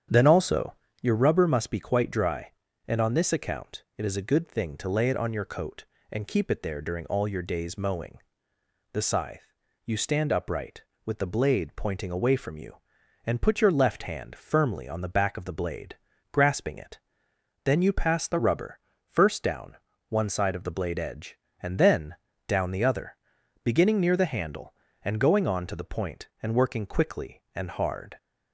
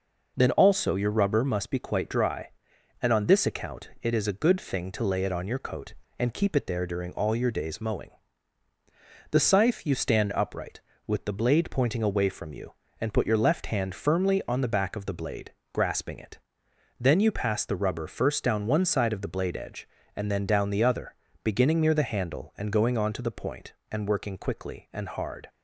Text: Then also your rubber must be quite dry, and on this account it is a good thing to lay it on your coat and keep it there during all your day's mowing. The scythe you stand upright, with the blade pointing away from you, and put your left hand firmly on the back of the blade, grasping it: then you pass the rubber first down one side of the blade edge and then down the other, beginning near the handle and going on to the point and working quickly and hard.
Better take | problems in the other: second | starts louder than the rest; strong; until 1.1 s; 8.5 dB // pauses between "also" and "your"; slight; at 0.7 s; 0.28 s long // pauses between "scythe" and "you"; slight; at 9.5 s; 0.32 s long // pauses between "rubber" and "first"; slight; at 18.7 s; 0.28 s long // pauses between "down" and "one"; slight; at 19.7 s; 0.32 s long // pauses between "then" and "down"; slight; at 22.1 s; 0.32 s long

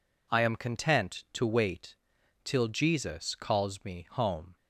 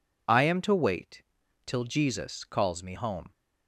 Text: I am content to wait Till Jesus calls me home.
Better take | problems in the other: first | skips "content"; at 0.6 s // pauses between "wait" and "Till"; at 1.2 s; 0.42 s long; noticeable in the first

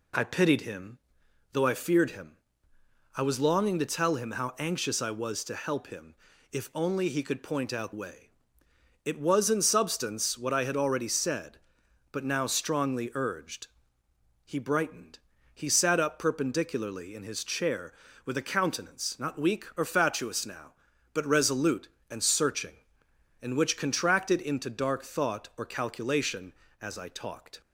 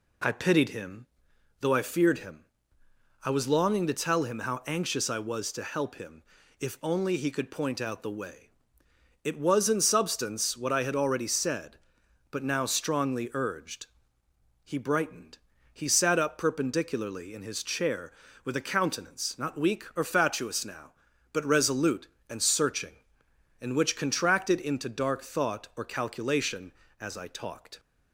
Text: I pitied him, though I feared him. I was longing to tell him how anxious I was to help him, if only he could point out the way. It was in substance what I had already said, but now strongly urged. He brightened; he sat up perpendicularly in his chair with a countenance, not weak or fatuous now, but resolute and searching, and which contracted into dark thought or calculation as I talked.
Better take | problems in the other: second | skips "the"; at 7.9 s

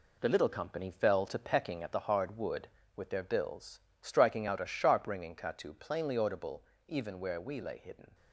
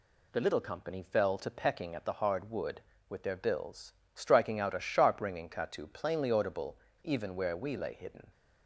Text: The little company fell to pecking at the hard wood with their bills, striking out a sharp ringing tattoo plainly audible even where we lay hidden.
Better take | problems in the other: second | gets quieter; throughout; 7 dB // pauses between "audible" and "even"; slight; at 6.6 s; 0.22 s long; slight in the second

